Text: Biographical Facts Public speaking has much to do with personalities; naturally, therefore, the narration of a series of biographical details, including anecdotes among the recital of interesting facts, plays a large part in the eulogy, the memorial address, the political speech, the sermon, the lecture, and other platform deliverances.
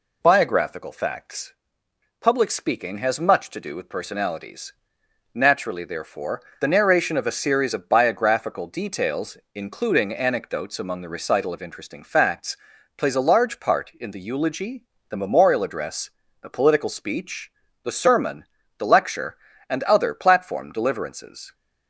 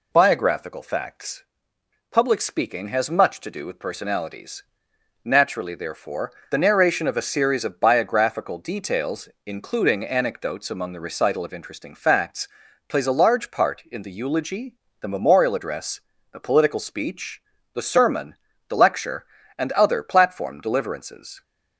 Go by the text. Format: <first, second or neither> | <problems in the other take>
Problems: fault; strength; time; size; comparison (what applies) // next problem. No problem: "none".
neither | pauses between "Facts" and "Public"; noticeable; the same in both